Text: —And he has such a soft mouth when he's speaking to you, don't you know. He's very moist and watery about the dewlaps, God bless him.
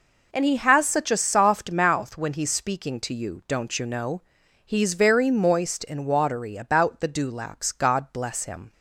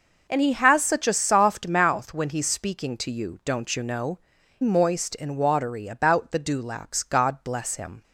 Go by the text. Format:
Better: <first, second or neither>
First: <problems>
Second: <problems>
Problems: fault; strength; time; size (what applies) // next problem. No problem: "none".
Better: first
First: none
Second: skips "He's very"; at 4.3 s